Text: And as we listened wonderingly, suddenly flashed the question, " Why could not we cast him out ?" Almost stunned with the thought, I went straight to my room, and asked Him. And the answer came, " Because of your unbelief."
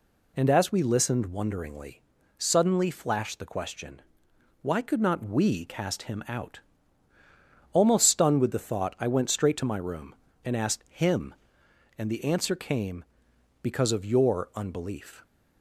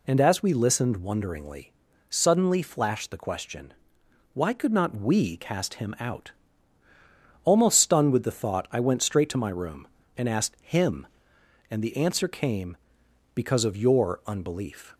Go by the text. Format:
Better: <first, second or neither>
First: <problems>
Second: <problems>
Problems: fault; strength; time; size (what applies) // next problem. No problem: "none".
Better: neither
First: none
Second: none